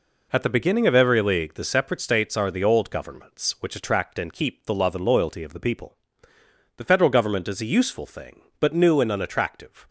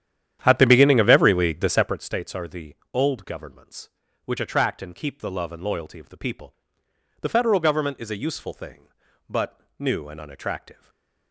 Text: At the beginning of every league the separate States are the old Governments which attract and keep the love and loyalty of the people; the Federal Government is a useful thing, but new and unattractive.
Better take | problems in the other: first | starts louder than the rest; strong; until 2.0 s; 10.5 dB // pauses between "the" and "old"; slight; at 2.7 s; 0.18 s long // pauses between "but" and "new"; slight; at 9.6 s; 0.16 s long // stays silent after the last word; slight; from 10.7 s on; 0.6 s long

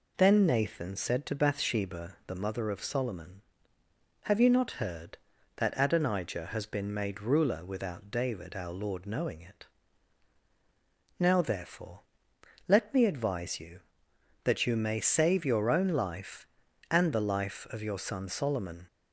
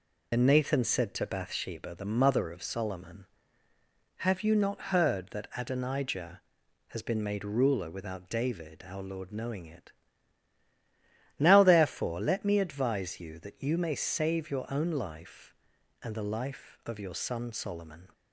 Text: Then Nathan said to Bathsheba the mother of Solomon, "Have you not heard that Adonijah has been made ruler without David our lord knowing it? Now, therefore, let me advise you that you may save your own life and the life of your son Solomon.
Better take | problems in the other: first | loses the start of "Then"; at 0.3 s; 80 ms

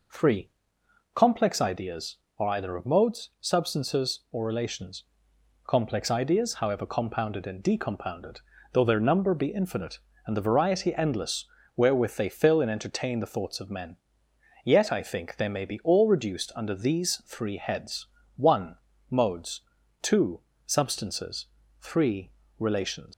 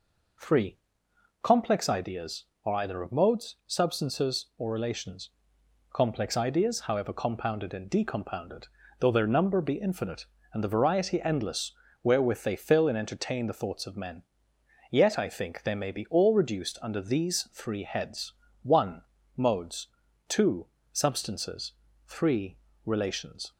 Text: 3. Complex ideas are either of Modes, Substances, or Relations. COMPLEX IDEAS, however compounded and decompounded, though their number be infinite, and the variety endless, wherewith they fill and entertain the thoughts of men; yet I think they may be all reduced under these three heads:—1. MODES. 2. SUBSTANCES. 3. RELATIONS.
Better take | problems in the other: second | leaves "RELATIONS" unfinished; at 23.1 s; 115 ms

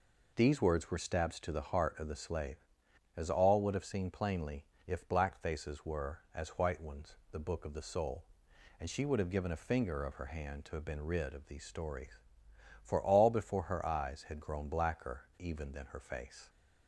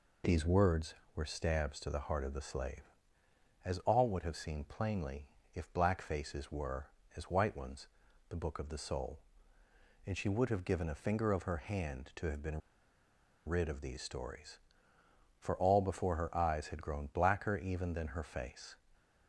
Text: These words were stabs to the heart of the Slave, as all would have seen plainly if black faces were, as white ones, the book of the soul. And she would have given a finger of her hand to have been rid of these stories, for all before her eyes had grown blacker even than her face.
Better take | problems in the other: first | pauses between "plainly" and "if"; slight; at 5.2 s; 0.26 s long; slight in the first // pauses between "been" and "rid"; noticeable; at 12.6 s; 0.88 s long

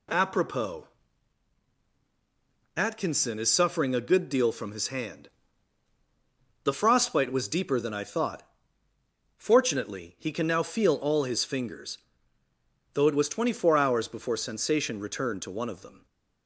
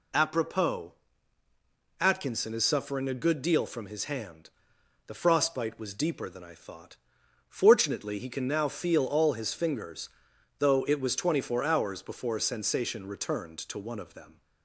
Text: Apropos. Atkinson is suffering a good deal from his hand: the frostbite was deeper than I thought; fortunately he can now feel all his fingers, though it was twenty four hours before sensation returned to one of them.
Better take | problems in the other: neither | none

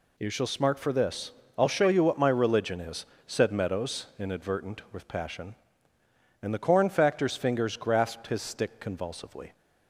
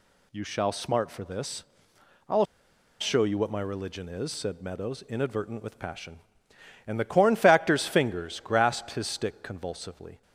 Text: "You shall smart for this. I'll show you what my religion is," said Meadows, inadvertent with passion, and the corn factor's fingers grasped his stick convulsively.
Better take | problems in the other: first | pauses between "I'll" and "show"; noticeable; at 2.4 s; 0.55 s long

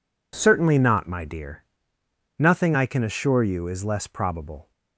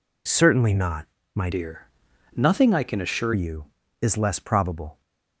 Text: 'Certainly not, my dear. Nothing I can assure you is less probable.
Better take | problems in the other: first | changes voice from "dear" to "assure"; from 1.5 to 3.3 s; 1.8 s long

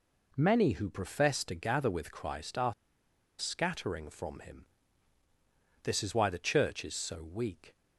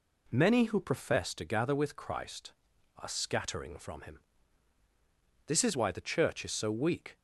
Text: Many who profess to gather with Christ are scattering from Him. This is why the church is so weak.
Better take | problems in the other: second | pauses between "are" and "scattering"; noticeable; at 2.7 s; 0.66 s long

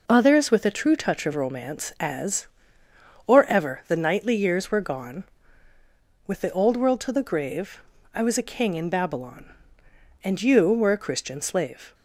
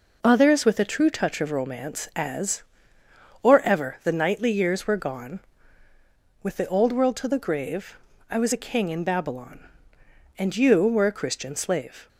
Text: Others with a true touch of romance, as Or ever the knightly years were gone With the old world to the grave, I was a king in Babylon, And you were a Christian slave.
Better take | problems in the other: neither | none

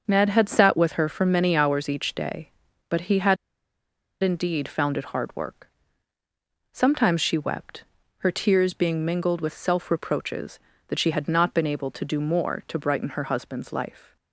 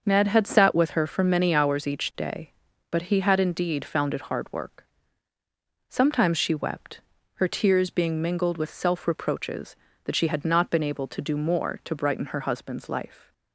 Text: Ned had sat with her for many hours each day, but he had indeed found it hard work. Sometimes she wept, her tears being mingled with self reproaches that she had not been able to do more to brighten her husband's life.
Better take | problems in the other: second | starts louder than the rest; until 1.0 s; 6.5 dB; also in the second // pauses between "had" and "indeed"; noticeable; at 3.3 s; 0.87 s long

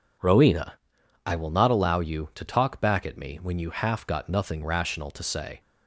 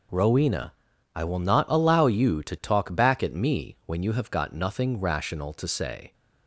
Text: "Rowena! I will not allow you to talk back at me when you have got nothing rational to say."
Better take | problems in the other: second | says "half" for "have"; at 3.6 s

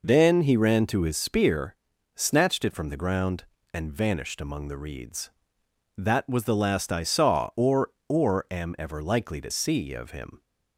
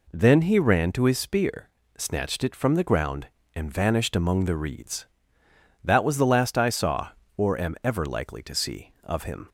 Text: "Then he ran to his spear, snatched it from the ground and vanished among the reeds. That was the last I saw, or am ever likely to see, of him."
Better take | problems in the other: second | says "or" twice; at 8.0 s

